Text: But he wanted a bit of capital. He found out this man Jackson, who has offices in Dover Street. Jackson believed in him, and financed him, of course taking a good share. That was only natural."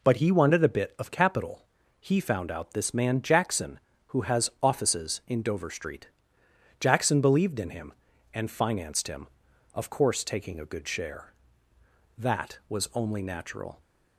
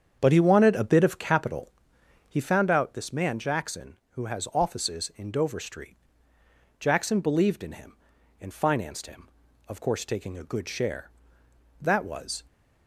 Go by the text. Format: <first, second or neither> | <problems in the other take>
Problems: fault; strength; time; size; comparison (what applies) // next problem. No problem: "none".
first | starts louder than the rest; strong; until 1.2 s; 8 dB // stops before "only natural"; at 12.4 s